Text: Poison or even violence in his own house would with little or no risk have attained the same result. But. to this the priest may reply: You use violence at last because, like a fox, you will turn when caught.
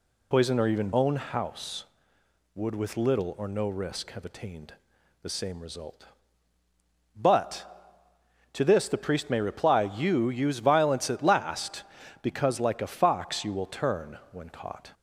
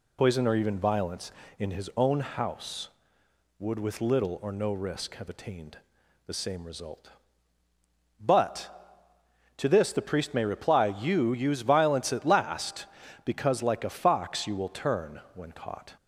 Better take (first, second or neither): second